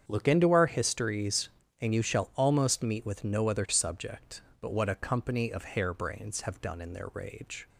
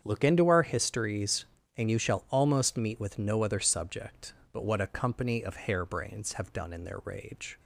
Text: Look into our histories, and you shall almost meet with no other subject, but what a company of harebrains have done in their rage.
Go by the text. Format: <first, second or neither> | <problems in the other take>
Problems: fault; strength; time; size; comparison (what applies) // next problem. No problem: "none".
neither | starts louder than the rest; strong; the same in both